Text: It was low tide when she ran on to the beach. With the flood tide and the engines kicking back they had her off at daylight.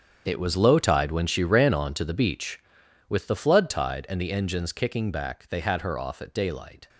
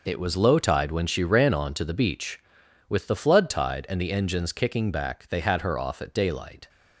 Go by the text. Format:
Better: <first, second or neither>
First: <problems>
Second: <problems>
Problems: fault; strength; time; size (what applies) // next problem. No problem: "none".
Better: second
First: gets quieter; strong; throughout; 13.5 dB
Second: none